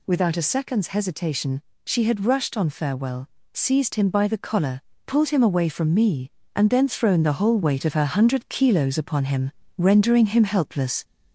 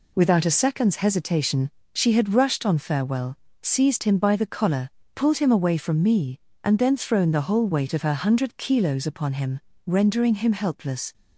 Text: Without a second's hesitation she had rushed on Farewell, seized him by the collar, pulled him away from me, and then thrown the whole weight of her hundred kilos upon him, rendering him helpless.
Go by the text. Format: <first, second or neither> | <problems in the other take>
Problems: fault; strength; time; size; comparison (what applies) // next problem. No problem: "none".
second | gets louder; slight; throughout; 2 dB // pauses between "hesitation" and "she"; slight; at 1.6 s; 0.22 s long; slight in the second